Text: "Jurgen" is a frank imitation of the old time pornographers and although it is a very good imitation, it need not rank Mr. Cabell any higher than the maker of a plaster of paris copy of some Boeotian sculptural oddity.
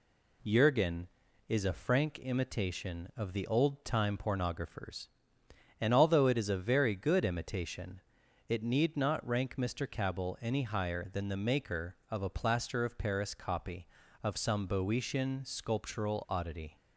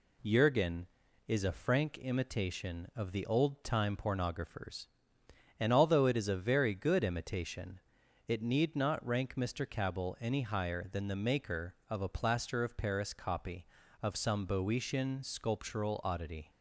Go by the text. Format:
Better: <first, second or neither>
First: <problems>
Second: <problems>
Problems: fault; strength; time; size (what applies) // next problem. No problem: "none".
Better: neither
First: none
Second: none